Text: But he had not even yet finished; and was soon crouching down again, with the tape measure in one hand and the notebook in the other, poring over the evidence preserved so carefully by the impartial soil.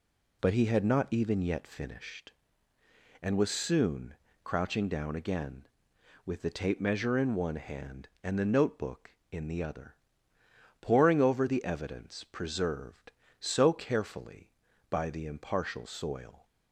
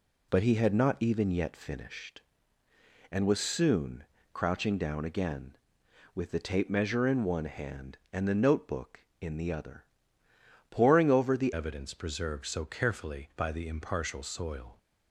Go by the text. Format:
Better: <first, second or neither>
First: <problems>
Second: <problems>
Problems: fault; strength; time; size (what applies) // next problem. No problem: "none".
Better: first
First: pauses between "soon" and "crouching"; slight; at 4.1 s; 0.28 s long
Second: pauses between "soon" and "crouching"; slight; at 4.0 s; 0.28 s long // changes voice at "evidence"; from 11.5 s on; 3.2 s long